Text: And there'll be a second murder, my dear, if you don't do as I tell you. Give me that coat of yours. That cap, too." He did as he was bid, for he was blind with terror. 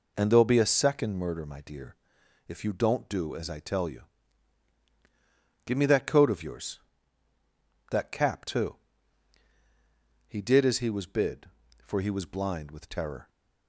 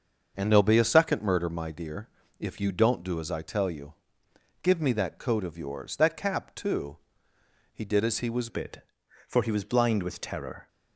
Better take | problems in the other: first | starts louder than the rest; until 1.3 s; 6.5 dB // changes voice at "bid"; from 8.4 s on; 2.2 s long

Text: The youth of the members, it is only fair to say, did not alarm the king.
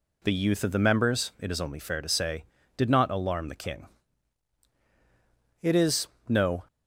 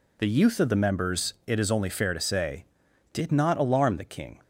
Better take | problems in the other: second | goes on to say "It is no"; noticeable; from 5.6 s on; 1.0 s long

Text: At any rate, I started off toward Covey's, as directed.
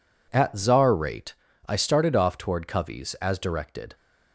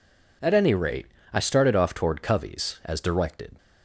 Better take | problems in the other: second | says "czar" for "any"; at 0.5 s

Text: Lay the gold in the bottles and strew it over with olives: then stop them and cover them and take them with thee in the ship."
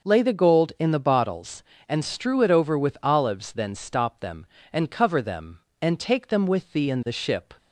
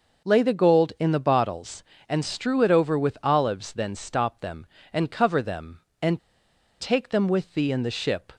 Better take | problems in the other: first | starts louder than the rest; noticeable; until 1.3 s; 6 dB; noticeable in the first // pauses between "and" and "take"; noticeable; at 6.1 s; 0.61 s long

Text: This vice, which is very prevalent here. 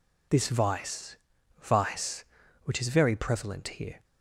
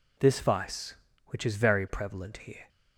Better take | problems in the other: second | says "vice" twice; at 1.6 s

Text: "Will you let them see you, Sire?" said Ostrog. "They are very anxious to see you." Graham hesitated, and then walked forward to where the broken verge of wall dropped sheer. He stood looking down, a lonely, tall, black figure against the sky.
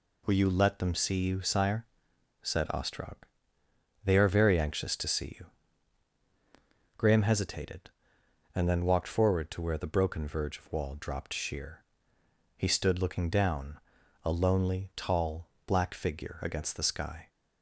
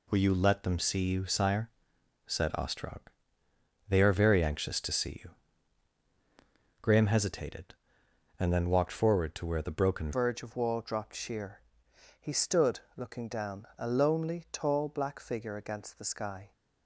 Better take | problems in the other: first | changes voice at "verge"; from 10.1 s on; 6.4 s long // pauses between "stood" and "looking"; slight; at 12.7 s; 0.18 s long

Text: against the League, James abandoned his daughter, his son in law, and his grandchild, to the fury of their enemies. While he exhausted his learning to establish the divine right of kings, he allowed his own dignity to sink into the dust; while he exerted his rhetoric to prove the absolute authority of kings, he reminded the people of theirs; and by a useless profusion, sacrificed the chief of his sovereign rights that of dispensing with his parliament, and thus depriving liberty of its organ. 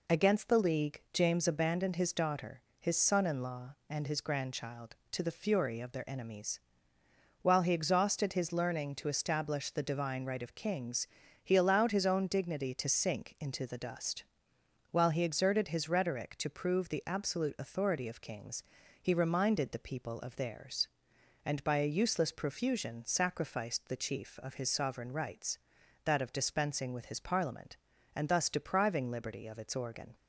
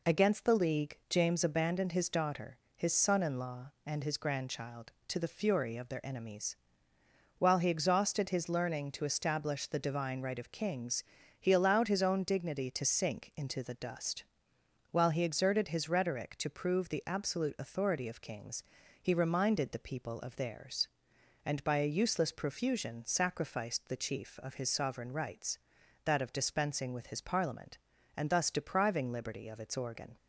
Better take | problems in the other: neither | none

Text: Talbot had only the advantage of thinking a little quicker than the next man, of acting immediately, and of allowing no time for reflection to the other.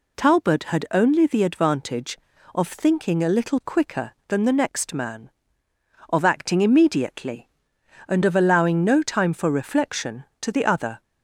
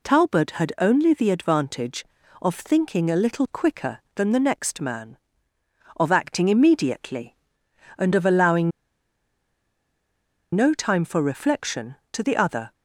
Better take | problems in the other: first | pauses between "allowing" and "no"; strong; at 8.7 s; 1.8 s long

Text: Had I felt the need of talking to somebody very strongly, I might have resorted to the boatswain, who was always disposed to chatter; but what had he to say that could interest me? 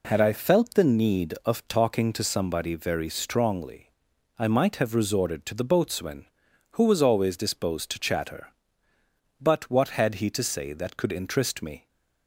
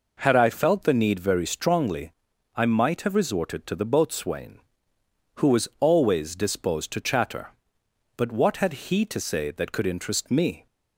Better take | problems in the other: first | skips "of talking to somebody"; at 1.2 s

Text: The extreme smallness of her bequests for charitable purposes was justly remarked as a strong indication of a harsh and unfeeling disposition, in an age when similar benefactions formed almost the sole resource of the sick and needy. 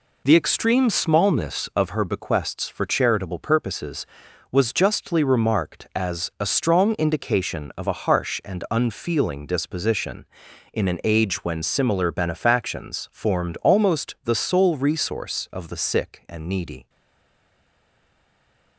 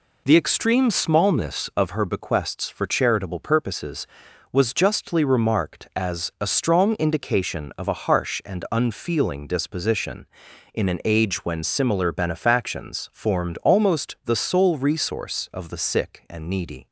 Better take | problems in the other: second | stays silent after the last word; noticeable; from 16.8 s on; 1.9 s long

